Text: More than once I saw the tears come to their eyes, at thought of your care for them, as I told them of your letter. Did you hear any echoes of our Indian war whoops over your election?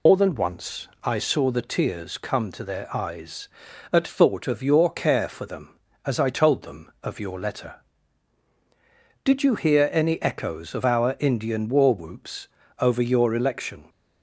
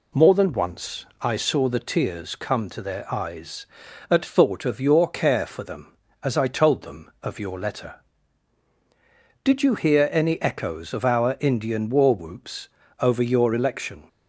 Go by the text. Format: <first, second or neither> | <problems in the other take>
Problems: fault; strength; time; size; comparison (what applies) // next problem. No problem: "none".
second | loses the start of "More"; at 0.0 s; 90 ms // pauses between "once" and "I"; slight; at 0.8 s; 0.16 s long; slight in the second // pauses between "whoops" and "over"; slight; at 12.4 s; 0.32 s long; slight in the second